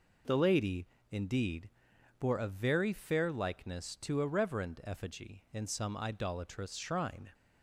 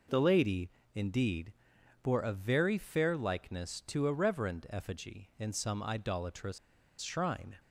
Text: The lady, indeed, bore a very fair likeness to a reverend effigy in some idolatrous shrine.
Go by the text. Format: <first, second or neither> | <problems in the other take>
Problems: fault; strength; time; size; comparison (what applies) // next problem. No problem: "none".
first | pauses between "idolatrous" and "shrine"; at 6.5 s; 0.43 s long